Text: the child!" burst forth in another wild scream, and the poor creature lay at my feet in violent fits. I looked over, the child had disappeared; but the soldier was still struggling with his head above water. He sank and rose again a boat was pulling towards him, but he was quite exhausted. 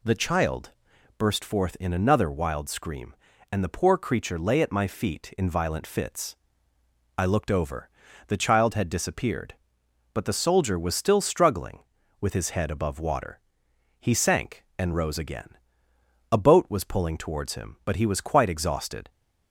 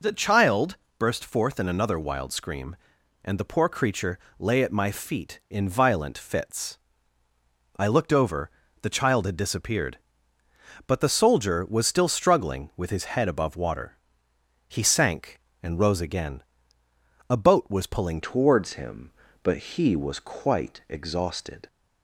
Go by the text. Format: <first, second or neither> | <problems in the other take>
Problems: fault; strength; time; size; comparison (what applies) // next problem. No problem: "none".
first | pauses between "creature" and "lay"; slight; at 4.1 s; 0.20 s long // pauses between "again" and "a"; noticeable; at 16.4 s; 0.88 s long; noticeable in the first // changes voice at "towards"; from 18.2 s on; 3.4 s long